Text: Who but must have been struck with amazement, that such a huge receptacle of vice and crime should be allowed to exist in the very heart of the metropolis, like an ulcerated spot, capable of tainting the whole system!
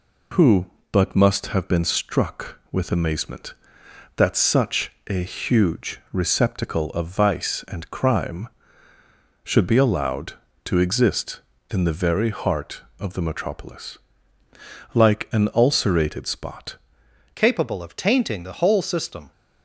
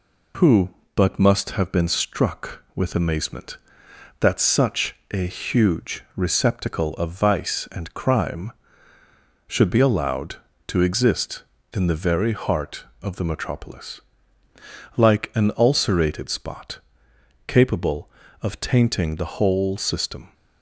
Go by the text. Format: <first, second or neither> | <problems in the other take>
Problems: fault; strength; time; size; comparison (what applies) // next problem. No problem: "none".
second | pauses between "such" and "a"; slight; at 4.9 s; 0.16 s long; slight in the second // changes voice at "capable"; from 17.3 s on; 2.0 s long